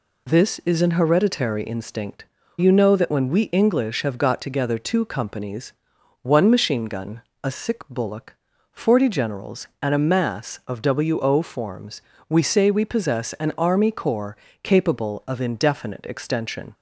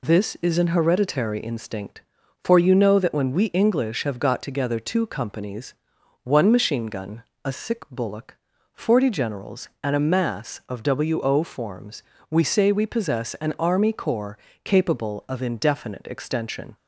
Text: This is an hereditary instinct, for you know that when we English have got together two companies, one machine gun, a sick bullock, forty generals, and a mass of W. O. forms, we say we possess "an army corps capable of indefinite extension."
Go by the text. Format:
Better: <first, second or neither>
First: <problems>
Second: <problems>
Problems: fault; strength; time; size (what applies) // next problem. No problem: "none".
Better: second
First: skips "for"; at 2.4 s // pauses between "corps" and "capable"; slight; at 14.3 s; 0.28 s long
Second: pauses between "corps" and "capable"; slight; at 14.3 s; 0.28 s long